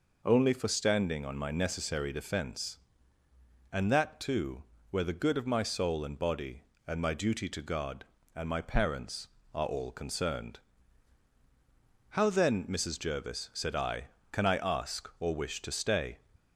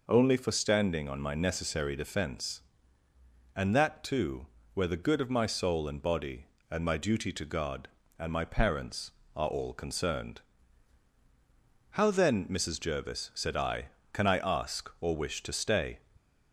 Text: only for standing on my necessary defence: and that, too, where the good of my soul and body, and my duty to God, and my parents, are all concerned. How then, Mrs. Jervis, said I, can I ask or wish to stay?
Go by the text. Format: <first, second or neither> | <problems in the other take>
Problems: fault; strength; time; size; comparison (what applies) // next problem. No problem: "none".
neither | none